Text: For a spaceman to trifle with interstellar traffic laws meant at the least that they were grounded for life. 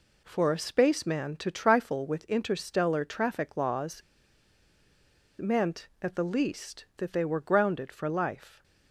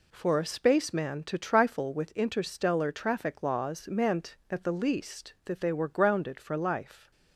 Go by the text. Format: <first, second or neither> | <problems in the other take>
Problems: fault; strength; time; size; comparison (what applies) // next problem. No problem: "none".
second | pauses between "laws" and "meant"; strong; at 4.0 s; 1.3 s long